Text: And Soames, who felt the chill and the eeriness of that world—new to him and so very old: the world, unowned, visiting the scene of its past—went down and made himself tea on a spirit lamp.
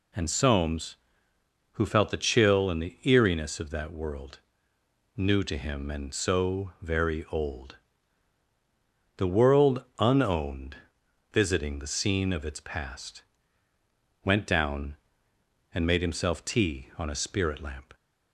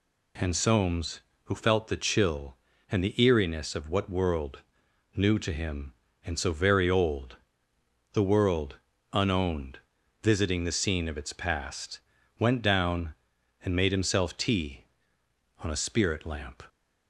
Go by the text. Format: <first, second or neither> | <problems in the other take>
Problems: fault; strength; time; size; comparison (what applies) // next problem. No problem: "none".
first | says "what" for "that"; at 3.8 s